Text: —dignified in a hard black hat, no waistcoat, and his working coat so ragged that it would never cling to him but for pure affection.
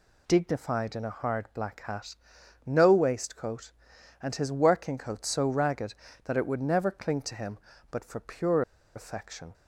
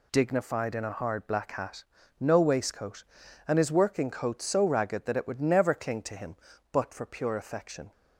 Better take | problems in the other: second | pauses between "pure" and "affection"; slight; at 8.6 s; 0.34 s long

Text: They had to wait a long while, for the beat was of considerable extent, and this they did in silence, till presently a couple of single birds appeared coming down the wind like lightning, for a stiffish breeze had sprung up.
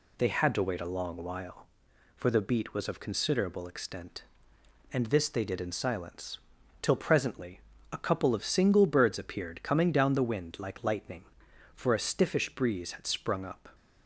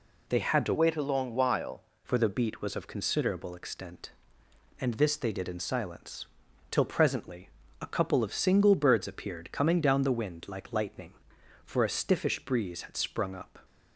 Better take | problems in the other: first | changes voice from "wait" to "while"; from 0.7 to 1.8 s; 1.1 s long // pauses between "presently" and "a"; slight; at 7.4 s; 0.32 s long; slight in the first

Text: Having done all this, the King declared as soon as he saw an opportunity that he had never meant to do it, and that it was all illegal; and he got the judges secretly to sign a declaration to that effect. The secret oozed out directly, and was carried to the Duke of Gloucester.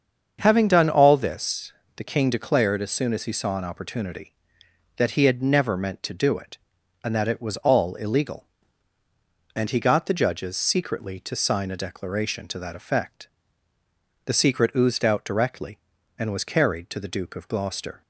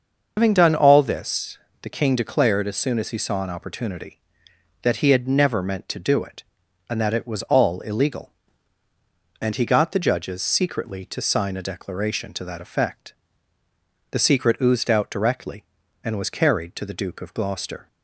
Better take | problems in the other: first | loses the start of "Having"; at 0.3 s; 130 ms // starts louder than the rest; until 1.3 s; 6.5 dB; also in the first

